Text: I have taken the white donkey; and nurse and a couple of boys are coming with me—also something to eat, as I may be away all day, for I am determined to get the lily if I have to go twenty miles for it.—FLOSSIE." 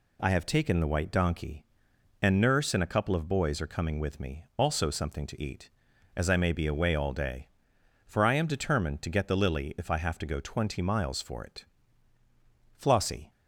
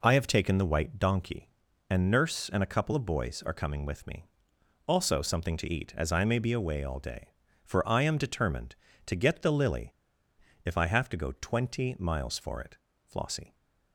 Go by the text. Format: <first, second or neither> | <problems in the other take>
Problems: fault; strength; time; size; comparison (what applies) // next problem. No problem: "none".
first | pauses between "lily" and "if"; noticeable; at 9.9 s; 0.70 s long